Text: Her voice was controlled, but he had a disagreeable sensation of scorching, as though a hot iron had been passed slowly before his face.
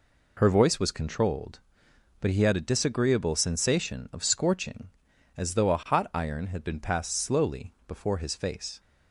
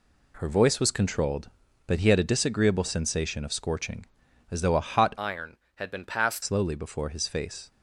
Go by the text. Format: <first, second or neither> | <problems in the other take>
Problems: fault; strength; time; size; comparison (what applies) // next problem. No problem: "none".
first | changes voice from "iron" to "passed"; from 5.1 to 6.4 s; 1.3 s long